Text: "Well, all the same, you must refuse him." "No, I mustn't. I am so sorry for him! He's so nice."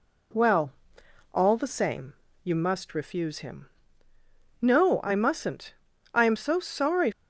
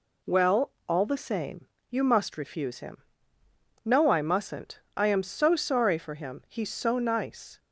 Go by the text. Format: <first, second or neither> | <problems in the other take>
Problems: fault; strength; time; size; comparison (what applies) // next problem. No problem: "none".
second | stops before "for him He's so nice"; at 7.1 s